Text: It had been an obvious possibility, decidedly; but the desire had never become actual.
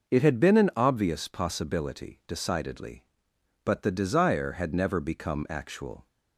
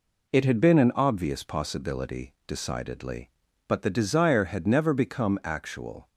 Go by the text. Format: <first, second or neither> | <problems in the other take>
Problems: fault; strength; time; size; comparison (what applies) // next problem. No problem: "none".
neither | none